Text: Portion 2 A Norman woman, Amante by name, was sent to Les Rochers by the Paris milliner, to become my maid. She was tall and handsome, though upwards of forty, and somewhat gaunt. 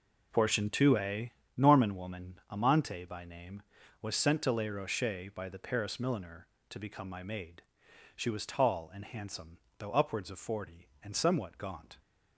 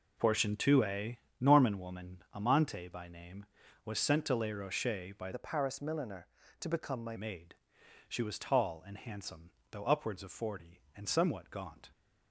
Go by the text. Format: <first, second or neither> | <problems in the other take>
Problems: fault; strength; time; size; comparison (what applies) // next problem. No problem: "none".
first | pauses between "A" and "Norman"; slight; at 1.1 s; 0.20 s long; slight in the first // changes voice from "the" to "my"; from 5.3 to 7.1 s; 1.8 s long